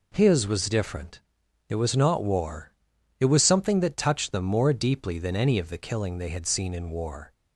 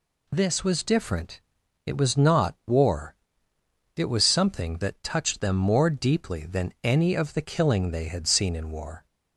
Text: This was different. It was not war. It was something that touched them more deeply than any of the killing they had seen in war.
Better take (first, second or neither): second